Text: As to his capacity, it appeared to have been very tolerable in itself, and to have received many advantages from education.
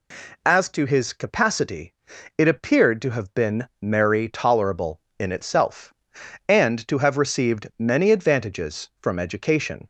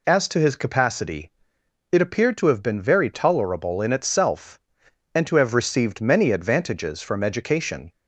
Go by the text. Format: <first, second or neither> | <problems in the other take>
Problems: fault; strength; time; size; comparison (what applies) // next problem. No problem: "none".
second | says "merry" for "very"; at 3.7 s